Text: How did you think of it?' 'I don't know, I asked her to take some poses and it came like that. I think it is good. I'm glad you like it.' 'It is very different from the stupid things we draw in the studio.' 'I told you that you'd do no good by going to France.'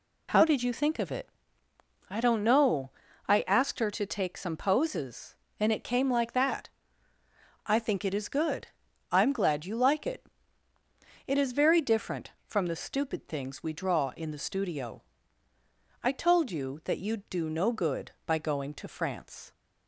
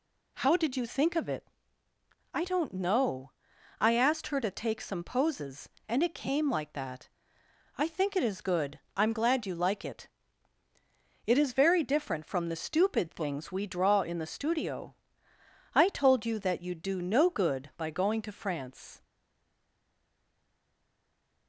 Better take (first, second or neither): first